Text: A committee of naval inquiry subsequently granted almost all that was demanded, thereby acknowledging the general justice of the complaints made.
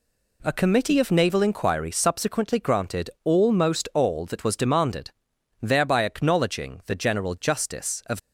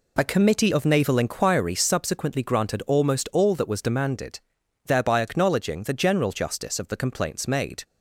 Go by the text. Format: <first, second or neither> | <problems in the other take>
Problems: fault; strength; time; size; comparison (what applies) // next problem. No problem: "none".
second | stops before "the complaints made"; at 8.1 s